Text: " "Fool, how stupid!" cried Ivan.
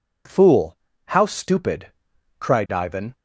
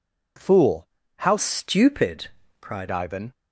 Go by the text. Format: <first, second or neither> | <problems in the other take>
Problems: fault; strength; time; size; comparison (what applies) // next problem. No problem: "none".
first | changes voice from "stupid" to "cried"; from 1.3 to 2.8 s; 1.5 s long